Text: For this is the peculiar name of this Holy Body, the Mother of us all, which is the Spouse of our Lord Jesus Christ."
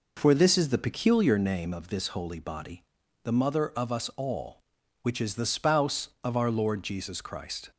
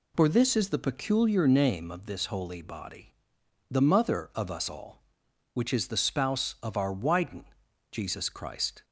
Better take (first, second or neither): first